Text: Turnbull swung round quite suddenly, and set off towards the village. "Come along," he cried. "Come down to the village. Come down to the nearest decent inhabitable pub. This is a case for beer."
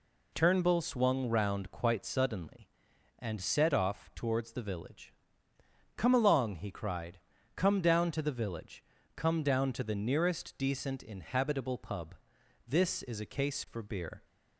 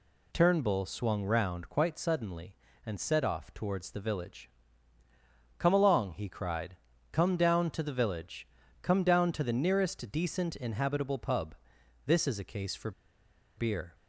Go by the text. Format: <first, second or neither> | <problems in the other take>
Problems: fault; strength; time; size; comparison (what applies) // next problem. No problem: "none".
first | pauses between "for" and "beer"; noticeable; at 12.9 s; 0.66 s long